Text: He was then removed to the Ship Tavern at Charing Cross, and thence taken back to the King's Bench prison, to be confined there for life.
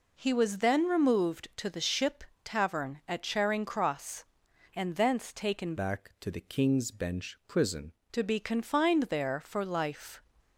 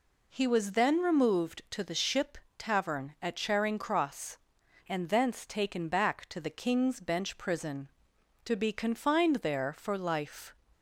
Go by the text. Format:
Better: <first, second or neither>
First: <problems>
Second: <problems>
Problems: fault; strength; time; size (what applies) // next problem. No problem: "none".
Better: second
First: pauses between "Ship" and "Tavern"; slight; at 2.2 s; 0.20 s long // changes voice from "back" to "prison"; from 5.7 to 7.9 s; 2.2 s long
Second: pauses between "Ship" and "Tavern"; slight; at 2.3 s; 0.20 s long